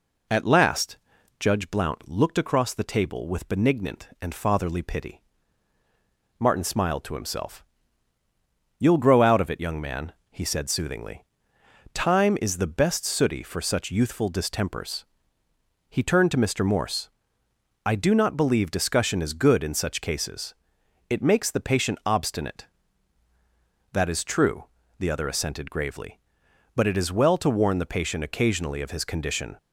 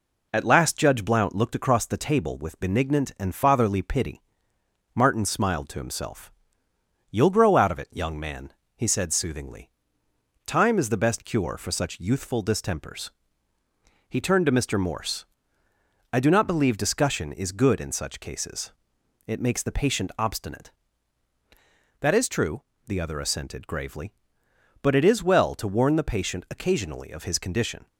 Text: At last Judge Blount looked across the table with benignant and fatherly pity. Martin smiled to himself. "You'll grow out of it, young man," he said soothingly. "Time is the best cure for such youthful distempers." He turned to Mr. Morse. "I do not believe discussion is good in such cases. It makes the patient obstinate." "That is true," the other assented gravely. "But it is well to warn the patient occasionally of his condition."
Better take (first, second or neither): second